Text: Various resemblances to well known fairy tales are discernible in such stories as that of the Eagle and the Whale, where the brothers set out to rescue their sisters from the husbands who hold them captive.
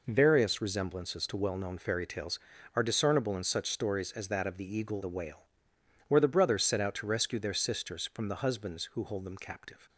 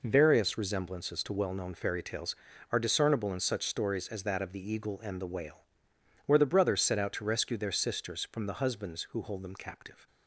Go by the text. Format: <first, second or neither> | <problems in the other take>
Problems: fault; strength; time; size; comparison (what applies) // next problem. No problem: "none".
second | skips "and"; at 5.0 s